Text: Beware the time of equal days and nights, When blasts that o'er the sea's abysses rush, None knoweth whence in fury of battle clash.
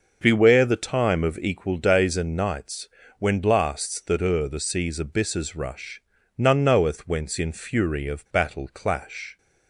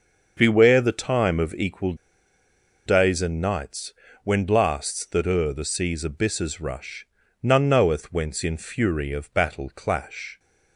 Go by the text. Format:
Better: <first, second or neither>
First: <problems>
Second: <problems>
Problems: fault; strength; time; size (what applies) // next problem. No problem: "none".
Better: first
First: starts louder than the rest; noticeable; until 1.2 s; 6 dB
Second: starts louder than the rest; until 1.3 s; 6.5 dB // pauses between "equal" and "days"; noticeable; at 1.9 s; 0.94 s long